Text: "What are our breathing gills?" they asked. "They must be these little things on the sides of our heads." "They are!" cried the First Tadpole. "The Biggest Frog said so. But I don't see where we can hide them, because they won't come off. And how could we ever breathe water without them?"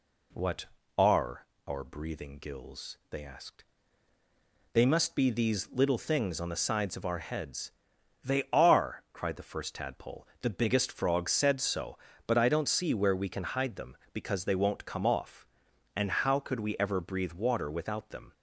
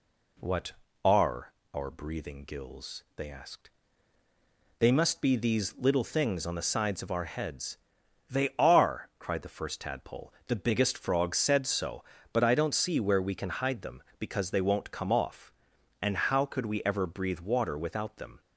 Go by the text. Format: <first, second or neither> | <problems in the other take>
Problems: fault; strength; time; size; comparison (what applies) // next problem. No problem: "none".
neither | pauses between "are" and "our"; slight; the same in both